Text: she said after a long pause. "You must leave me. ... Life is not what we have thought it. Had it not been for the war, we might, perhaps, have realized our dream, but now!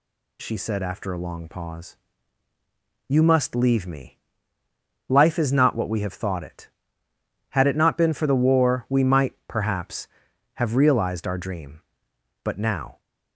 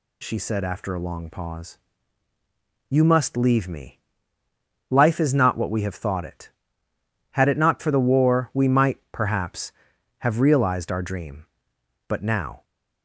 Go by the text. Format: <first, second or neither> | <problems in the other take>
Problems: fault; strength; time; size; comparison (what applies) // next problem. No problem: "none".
first | skips "been"; at 7.7 s